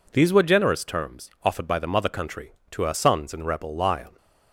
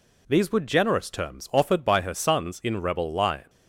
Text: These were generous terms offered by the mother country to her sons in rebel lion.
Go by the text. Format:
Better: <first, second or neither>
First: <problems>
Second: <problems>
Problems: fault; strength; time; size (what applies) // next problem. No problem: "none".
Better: first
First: none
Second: skips "the mother country to"; at 2.0 s